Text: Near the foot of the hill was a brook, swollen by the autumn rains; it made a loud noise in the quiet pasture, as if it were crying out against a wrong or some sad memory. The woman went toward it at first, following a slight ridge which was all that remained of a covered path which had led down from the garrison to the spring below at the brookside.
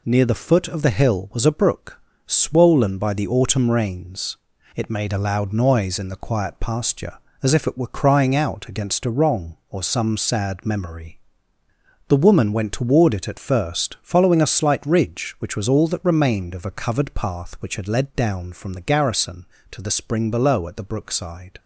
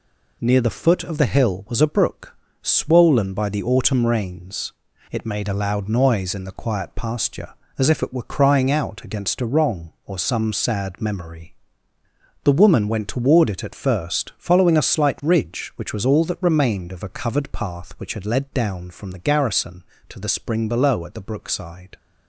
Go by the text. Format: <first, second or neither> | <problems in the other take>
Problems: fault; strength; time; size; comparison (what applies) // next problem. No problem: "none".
neither | none